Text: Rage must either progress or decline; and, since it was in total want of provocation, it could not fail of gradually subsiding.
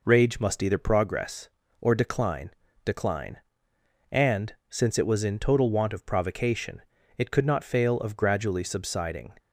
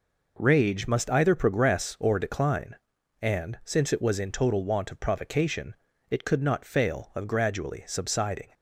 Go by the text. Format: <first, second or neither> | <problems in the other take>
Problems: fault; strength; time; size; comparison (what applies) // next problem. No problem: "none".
second | says "decline" twice; at 2.8 s